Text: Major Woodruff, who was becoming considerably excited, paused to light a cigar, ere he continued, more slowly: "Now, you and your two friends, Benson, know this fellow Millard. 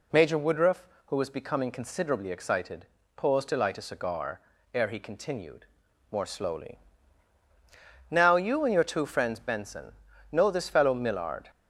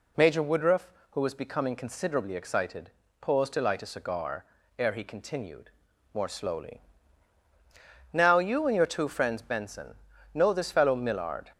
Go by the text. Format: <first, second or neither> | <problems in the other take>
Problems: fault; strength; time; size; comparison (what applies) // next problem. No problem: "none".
neither | none